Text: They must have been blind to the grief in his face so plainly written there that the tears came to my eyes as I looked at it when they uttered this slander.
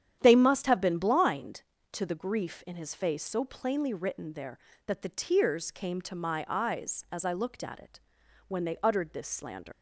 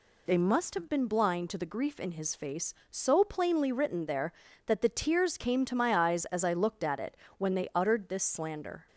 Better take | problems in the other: second | starts louder than the rest; strong; until 1.2 s; 9.5 dB // pauses between "it" and "when"; noticeable; at 8.0 s; 0.48 s long; slight in the second // leaves "slander" unfinished; at 9.7 s; 115 ms

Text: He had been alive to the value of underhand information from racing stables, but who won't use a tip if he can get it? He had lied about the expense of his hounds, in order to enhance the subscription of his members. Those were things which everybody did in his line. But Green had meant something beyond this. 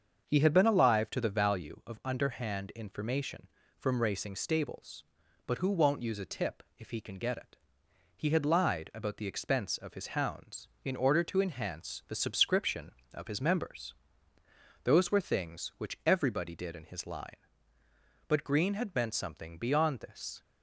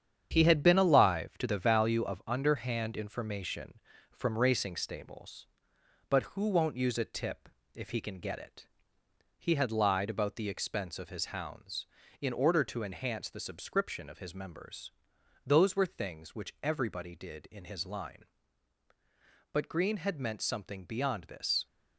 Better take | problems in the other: first | gets quieter; strong; throughout; 7.5 dB // starts louder than the rest; strong; until 1.3 s; 8.5 dB; also in the first // pauses between "tip" and "if"; slight; at 7.4 s; 0.24 s long; slight in the first

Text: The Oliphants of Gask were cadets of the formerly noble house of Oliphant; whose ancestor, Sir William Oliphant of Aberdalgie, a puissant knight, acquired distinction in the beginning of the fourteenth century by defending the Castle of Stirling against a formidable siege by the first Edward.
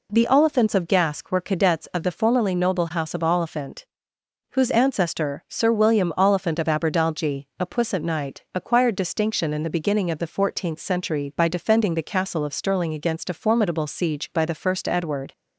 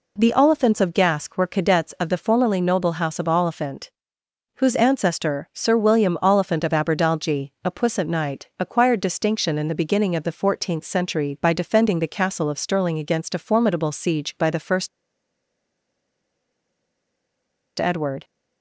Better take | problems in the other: first | pauses between "first" and "Edward"; strong; at 14.8 s; 2.8 s long

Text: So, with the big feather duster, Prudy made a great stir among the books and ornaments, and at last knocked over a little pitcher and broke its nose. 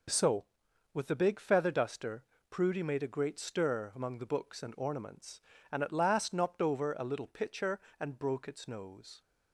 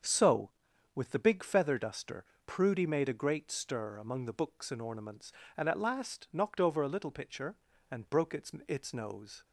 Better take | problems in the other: first | starts louder than the rest; until 1.5 s; 7 dB // says "its" twice; at 8.6 s

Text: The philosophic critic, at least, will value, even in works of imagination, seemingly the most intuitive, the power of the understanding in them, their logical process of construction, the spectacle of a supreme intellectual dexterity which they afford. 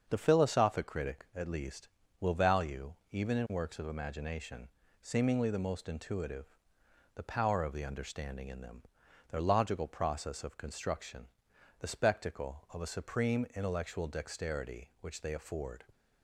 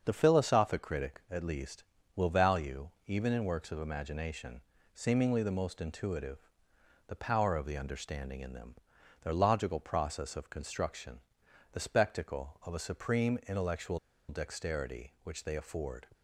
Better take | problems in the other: first | starts louder than the rest; until 1.0 s; 6.5 dB; also in the first // pauses between "intellectual" and "dexterity"; slight; at 13.9 s; 0.31 s long

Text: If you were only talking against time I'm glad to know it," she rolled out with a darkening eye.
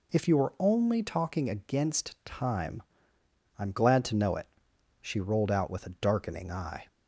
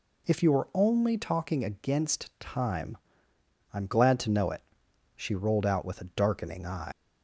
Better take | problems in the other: first | pauses between "time" and "I'm"; noticeable; at 2.9 s; 0.74 s long; noticeable in the first // leaves "eye" unfinished; at 6.9 s; 100 ms

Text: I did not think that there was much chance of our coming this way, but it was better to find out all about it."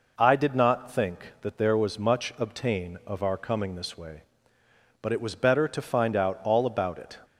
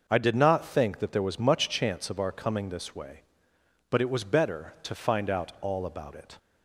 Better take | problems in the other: second | says "obtain" for "chance"; at 2.3 s

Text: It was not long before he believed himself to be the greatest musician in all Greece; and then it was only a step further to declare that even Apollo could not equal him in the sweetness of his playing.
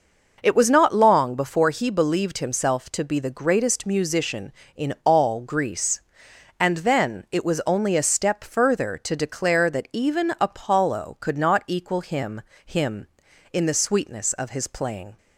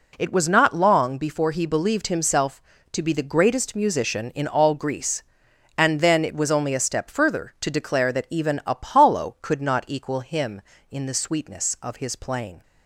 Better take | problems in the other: second | says "him" twice; at 12.6 s

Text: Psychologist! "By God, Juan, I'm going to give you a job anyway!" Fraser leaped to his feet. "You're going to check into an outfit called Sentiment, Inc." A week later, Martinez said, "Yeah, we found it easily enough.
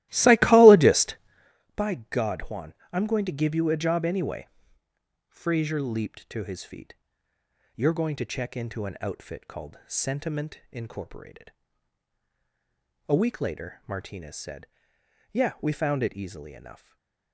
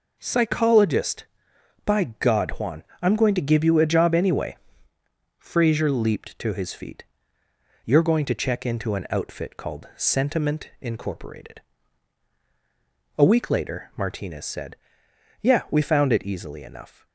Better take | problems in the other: second | starts louder than the rest; strong; until 1.5 s; 16.5 dB // stays silent after the last word; slight; from 16.7 s on; 0.6 s long

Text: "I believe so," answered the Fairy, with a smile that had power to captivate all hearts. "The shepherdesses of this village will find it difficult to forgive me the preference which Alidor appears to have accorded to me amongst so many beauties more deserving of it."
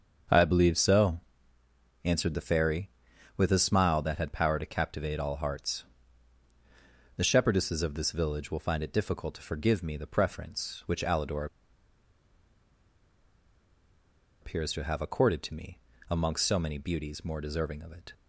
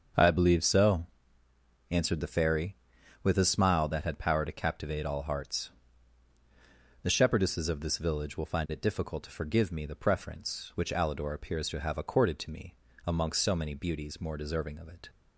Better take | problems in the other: second | starts louder than the rest; strong; until 2.1 s; 7 dB; strong in the second // pauses between "Alidor" and "appears"; strong; at 11.4 s; 2.9 s long // pauses between "me" and "amongst"; slight; at 15.7 s; 0.32 s long; slight in the second

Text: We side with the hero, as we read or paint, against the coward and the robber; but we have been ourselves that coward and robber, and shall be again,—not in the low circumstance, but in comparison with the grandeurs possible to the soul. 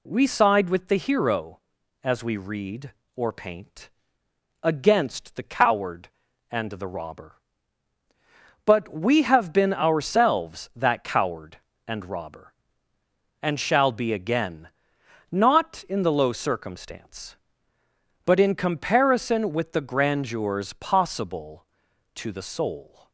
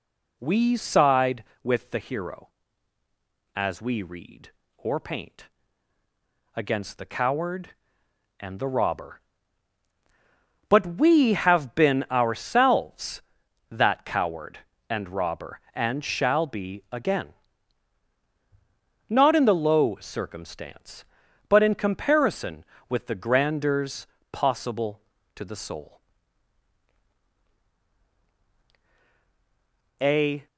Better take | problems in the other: first | pauses between "grandeurs" and "possible"; slight; at 24.0 s; 0.26 s long // goes on to say "A"; slight; from 29.9 s on; 0.48 s long

